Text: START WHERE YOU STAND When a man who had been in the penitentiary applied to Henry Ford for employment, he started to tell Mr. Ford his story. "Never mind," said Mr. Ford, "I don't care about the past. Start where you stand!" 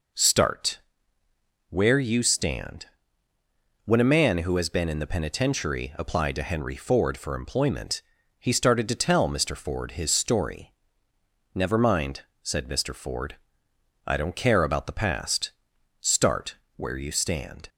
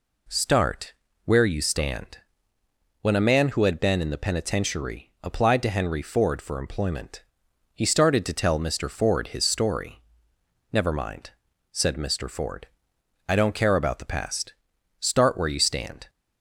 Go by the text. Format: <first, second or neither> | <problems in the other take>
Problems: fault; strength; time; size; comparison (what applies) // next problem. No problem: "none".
second | pauses between "START" and "WHERE"; noticeable; at 0.8 s; 0.88 s long; slight in the second // pauses between "STAND" and "When"; noticeable; at 2.8 s; 0.98 s long; noticeable in the second // says "has" for "had"; at 4.5 s // pauses between "Start" and "where"; slight; at 16.5 s; 0.18 s long